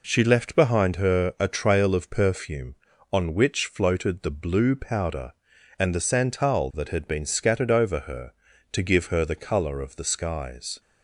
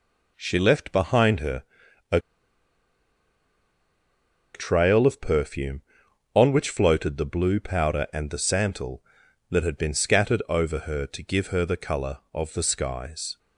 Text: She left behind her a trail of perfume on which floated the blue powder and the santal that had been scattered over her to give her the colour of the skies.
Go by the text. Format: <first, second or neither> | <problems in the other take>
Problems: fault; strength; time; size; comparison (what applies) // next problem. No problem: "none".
first | pauses between "her" and "a"; noticeable; at 1.6 s; 0.48 s long // pauses between "a" and "trail"; strong; at 2.1 s; 2.3 s long